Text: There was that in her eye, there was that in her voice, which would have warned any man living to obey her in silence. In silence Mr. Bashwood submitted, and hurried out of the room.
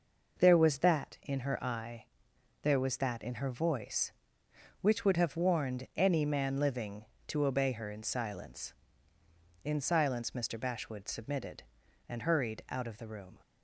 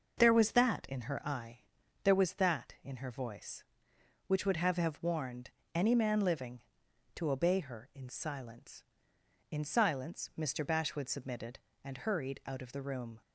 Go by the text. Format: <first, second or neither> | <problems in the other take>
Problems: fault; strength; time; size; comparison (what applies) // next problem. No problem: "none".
first | says "have" twice; at 4.7 s // pauses between "warned" and "any"; slight; at 5.5 s; 0.22 s long